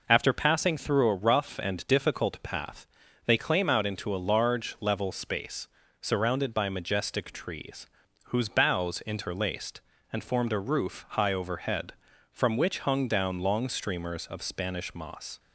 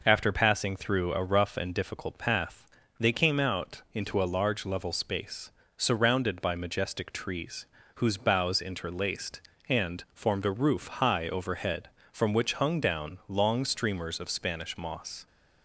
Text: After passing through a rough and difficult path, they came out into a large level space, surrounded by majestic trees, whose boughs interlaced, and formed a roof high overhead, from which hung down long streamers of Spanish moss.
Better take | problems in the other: second | says "claim" for "came"; at 3.3 s

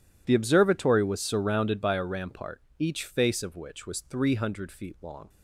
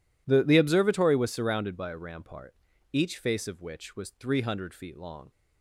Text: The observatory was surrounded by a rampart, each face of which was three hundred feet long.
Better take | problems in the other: first | says "The" twice; at 0.4 s

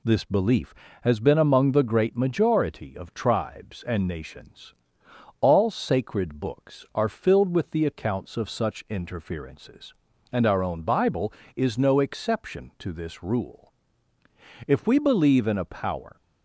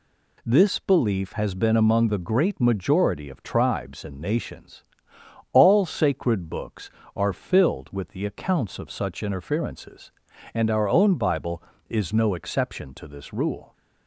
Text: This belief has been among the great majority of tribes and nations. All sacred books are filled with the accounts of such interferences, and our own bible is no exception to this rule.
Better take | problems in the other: second | goes on to say "If we believe in a power"; from 14.6 s on; 1.5 s long

